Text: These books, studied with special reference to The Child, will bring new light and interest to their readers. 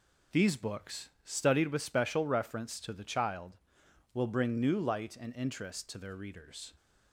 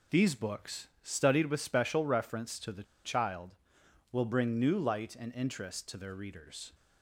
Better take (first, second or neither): first